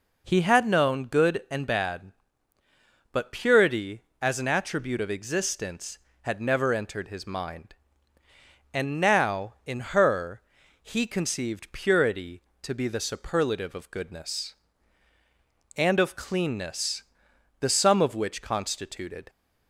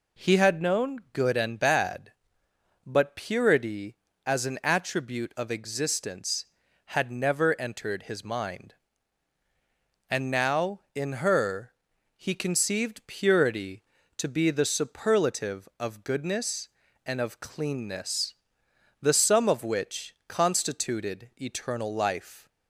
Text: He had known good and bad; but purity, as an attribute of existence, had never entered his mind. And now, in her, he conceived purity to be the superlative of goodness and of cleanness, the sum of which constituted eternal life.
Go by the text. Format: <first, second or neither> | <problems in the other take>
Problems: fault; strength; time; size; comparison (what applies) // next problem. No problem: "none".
second | stops before "eternal life"; at 19.2 s